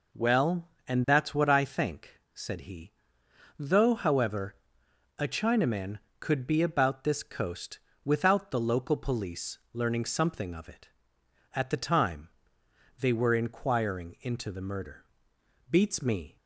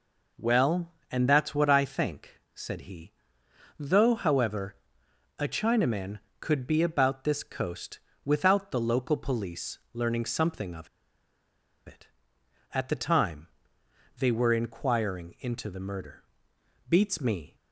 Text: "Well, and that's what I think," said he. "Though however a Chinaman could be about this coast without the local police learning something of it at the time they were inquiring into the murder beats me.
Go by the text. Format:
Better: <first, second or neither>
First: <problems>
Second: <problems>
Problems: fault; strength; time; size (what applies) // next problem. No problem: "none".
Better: first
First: pauses between "however" and "a"; noticeable; at 4.5 s; 0.62 s long // pauses between "coast" and "without"; slight; at 7.7 s; 0.26 s long // pauses between "police" and "learning"; slight; at 9.5 s; 0.16 s long // pauses between "time" and "they"; noticeable; at 12.2 s; 0.70 s long // pauses between "murder" and "beats"; noticeable; at 15.0 s; 0.64 s long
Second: pauses between "however" and "a"; noticeable; at 4.7 s; 0.62 s long // pauses between "coast" and "without"; slight; at 7.9 s; 0.26 s long // pauses between "police" and "learning"; slight; at 9.7 s; 0.16 s long // pauses between "of" and "it"; at 10.8 s; 0.99 s long // pauses between "time" and "they"; noticeable; at 13.4 s; 0.70 s long // pauses between "murder" and "beats"; noticeable; at 16.2 s; 0.64 s long